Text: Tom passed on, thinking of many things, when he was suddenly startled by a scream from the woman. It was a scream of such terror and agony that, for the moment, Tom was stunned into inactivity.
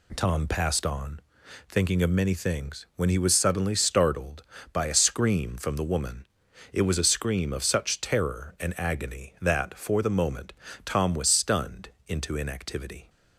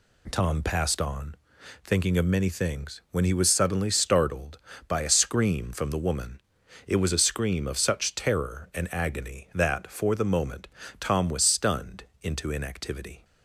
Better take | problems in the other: neither | pauses between "stunned" and "into"; slight; the same in both

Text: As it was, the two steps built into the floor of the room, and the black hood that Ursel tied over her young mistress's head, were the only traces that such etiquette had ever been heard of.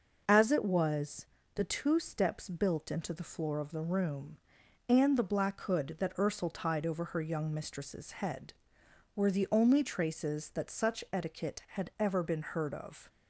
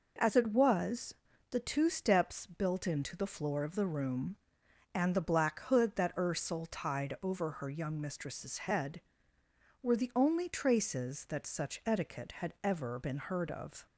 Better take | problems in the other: neither | none

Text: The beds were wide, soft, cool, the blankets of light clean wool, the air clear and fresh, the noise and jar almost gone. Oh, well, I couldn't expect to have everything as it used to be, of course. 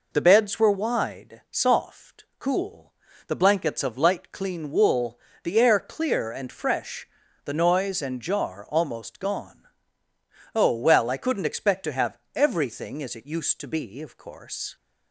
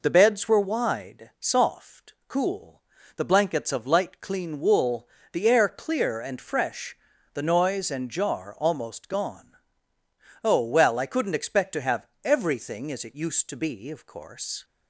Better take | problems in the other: neither | pauses between "have" and "everything"; slight; the same in both

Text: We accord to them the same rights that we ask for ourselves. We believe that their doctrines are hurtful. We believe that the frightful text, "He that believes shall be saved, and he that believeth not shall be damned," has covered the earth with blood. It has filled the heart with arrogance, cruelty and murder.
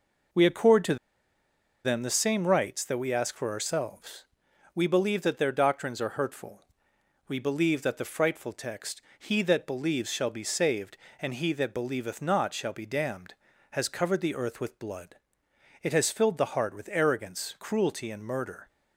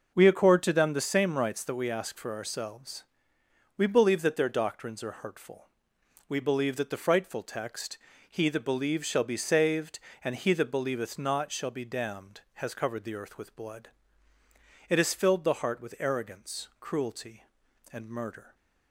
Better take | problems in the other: second | pauses between "to" and "them"; noticeable; at 0.9 s; 0.89 s long

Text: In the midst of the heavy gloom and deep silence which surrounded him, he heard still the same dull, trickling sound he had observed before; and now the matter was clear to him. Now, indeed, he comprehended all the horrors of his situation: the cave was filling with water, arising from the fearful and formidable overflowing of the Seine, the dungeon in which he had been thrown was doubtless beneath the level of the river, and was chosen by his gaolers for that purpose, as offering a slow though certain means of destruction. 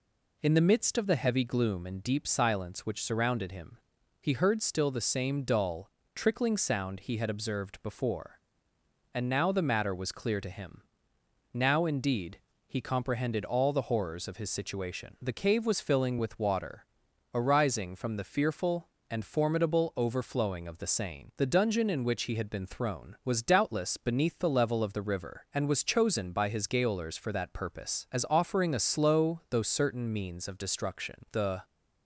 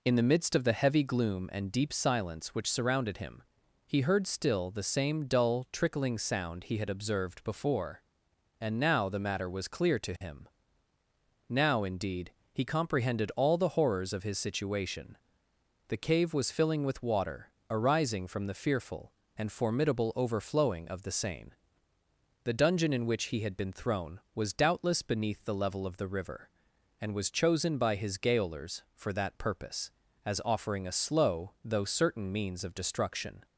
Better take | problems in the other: second | goes on to say "The"; slight; from 31.3 s on; 0.30 s long

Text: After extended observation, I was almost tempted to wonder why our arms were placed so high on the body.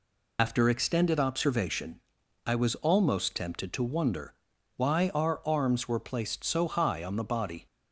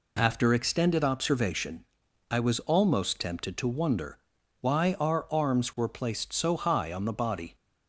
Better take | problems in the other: second | loses the start of "After"; at 0.3 s; 75 ms // pauses between "wonder" and "why"; at 4.3 s; 0.44 s long; also in the second

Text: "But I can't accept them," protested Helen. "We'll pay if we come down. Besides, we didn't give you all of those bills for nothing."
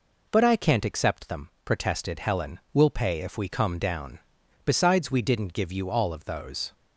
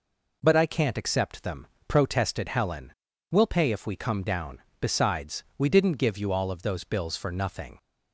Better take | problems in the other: second | stops before "bills for nothing"; at 6.7 s

